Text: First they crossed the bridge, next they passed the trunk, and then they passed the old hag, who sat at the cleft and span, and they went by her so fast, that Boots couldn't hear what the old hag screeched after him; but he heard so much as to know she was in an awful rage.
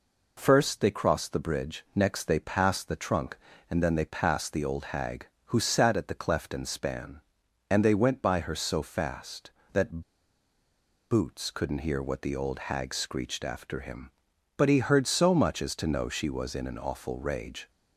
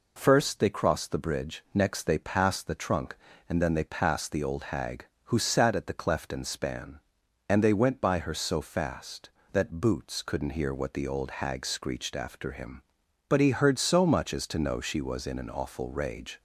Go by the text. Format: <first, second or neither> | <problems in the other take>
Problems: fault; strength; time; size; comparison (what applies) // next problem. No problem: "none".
second | pauses between "that" and "Boots"; at 10.0 s; 1.1 s long